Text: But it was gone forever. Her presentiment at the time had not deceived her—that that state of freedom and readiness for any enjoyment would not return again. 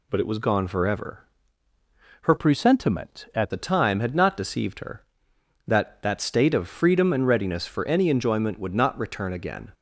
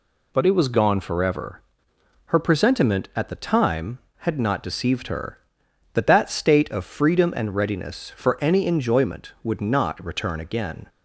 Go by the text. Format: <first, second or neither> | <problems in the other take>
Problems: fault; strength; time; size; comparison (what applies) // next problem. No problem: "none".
second | changes voice from "presentiment" to "at"; from 2.3 to 3.5 s; 1.2 s long